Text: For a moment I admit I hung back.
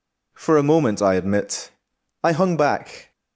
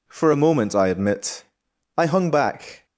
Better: neither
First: pauses between "admit" and "I"; noticeable; at 1.6 s; 0.54 s long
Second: pauses between "admit" and "I"; noticeable; at 1.4 s; 0.54 s long

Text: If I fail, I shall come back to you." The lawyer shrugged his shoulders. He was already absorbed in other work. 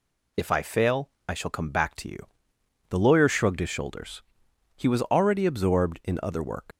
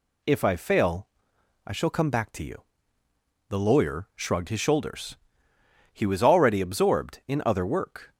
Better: second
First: leaves "work" unfinished; at 6.7 s; 75 ms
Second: none

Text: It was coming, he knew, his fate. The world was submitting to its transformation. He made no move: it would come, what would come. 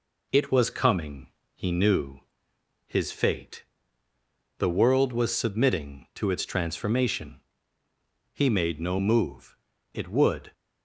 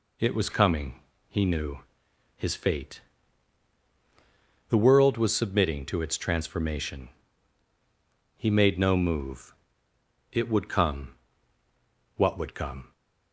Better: second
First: stops before "come what would come"; at 10.5 s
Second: none

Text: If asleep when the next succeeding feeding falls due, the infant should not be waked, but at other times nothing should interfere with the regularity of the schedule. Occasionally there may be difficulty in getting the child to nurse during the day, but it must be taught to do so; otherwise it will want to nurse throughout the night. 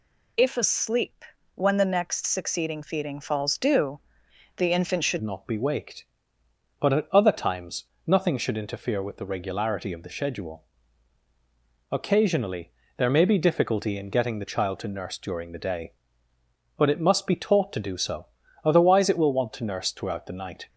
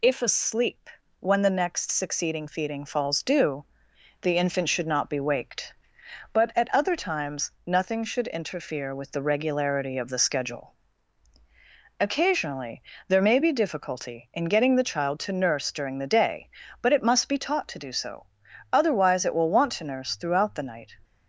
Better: second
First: pauses between "asleep" and "when"; slight; at 1.2 s; 0.30 s long // changes voice at "not"; from 5.2 s on; 15.4 s long // pauses between "times" and "nothing"; slight; at 7.8 s; 0.22 s long // pauses between "Occasionally" and "there"; slight; at 12.7 s; 0.28 s long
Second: pauses between "asleep" and "when"; slight; at 0.9 s; 0.30 s long // pauses between "Occasionally" and "there"; slight; at 12.8 s; 0.26 s long

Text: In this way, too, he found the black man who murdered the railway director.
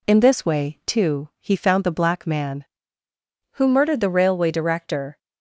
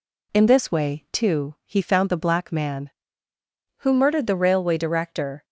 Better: neither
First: none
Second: none

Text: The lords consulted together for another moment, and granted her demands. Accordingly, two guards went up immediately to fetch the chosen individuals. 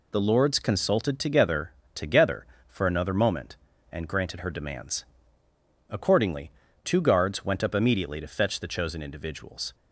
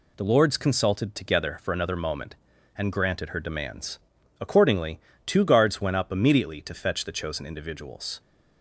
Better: second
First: says "together" twice; at 1.9 s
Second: none

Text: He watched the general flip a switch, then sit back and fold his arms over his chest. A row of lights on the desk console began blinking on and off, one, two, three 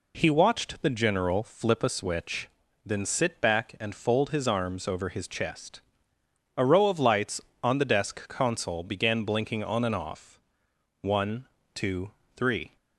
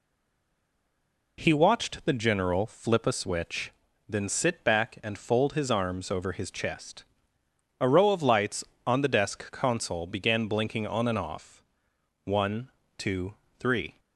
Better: first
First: none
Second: stays silent before the first word; noticeable; until 1.3 s; 1.3 s long

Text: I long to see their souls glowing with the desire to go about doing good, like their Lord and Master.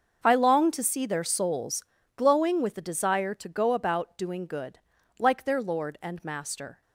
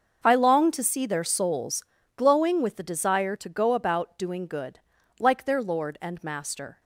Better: neither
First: starts louder than the rest; until 1.2 s; 6.5 dB // pauses between "souls" and "glowing"; slight; at 1.8 s; 0.32 s long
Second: starts louder than the rest; until 1.2 s; 6.5 dB // pauses between "souls" and "glowing"; slight; at 1.8 s; 0.32 s long

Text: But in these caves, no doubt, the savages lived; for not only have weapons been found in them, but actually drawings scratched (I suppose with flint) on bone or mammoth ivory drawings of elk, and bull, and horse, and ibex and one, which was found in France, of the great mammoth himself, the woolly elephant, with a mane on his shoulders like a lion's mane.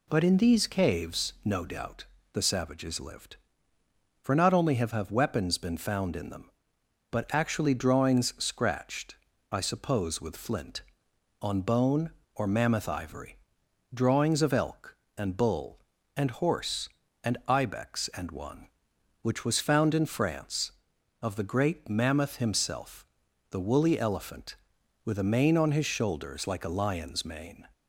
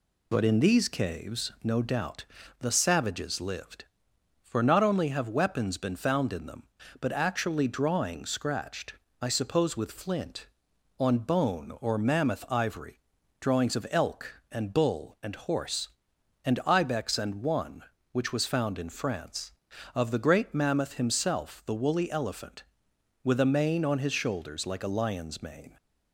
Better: second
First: says "have" twice; at 4.9 s // pauses between "ivory" and "drawings"; noticeable; at 13.3 s; 0.56 s long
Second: pauses between "ivory" and "drawings"; at 13.0 s; 0.38 s long

